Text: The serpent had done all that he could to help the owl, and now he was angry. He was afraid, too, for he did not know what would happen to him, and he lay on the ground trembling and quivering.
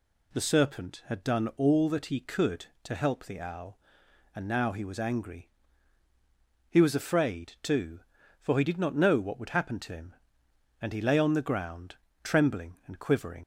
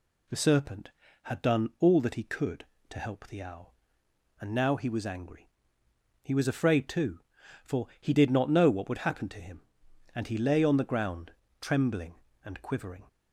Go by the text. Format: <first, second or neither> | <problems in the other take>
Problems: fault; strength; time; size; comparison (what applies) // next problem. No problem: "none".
second | pauses between "ground" and "trembling"; slight; at 11.9 s; 0.28 s long; slight in the second // leaves "quivering" unfinished; at 13.4 s; 60 ms